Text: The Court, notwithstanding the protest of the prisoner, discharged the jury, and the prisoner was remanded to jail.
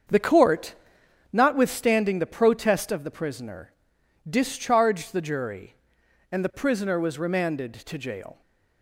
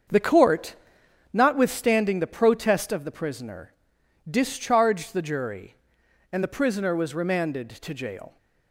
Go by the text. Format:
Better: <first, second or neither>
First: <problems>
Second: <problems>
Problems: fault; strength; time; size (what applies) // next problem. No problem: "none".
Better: neither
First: starts louder than the rest; until 1.7 s; 7 dB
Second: starts louder than the rest; until 1.7 s; 7 dB